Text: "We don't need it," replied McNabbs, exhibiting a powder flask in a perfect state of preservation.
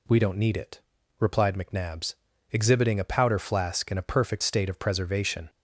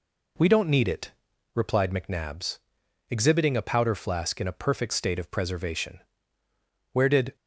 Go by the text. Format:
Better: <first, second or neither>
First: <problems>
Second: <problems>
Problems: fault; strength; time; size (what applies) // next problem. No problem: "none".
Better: first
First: none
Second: goes on to say "Where did"; slight; from 6.9 s on; 0.44 s long